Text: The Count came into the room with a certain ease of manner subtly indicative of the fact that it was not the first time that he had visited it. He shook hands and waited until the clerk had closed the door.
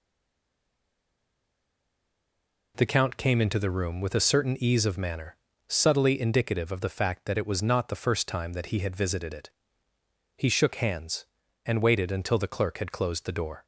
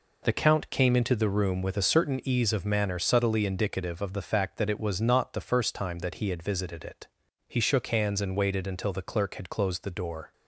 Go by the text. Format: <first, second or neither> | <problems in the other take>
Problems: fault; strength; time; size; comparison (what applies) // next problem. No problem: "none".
second | stays silent before the first word; strong; until 2.7 s; 2.7 s long // pauses between "manner" and "subtly"; slight; at 5.3 s; 0.32 s long